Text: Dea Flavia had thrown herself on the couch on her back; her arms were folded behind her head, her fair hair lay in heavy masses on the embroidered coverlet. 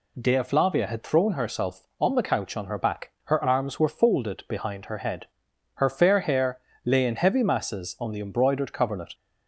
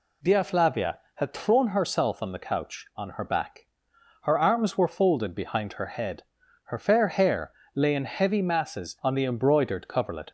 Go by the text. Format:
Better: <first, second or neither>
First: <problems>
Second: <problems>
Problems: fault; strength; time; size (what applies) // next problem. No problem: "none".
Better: neither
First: pauses between "hair" and "lay"; slight; at 6.6 s; 0.24 s long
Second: pauses between "hair" and "lay"; slight; at 7.5 s; 0.22 s long